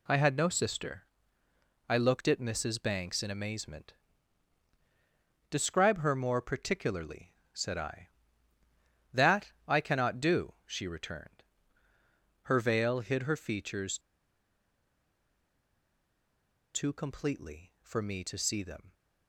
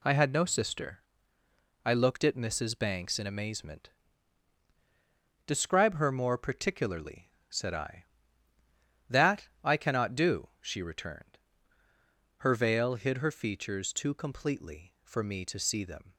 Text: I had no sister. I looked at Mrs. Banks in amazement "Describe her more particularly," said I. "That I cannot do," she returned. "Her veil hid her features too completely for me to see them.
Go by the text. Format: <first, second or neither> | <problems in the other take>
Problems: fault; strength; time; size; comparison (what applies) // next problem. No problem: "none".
second | pauses between "amazement" and "Describe"; strong; at 3.9 s; 1.5 s long; strong in the second // pauses between "That" and "I"; slight; at 9.5 s; 0.16 s long; slight in the second // pauses between "features" and "too"; strong; at 13.9 s; 2.7 s long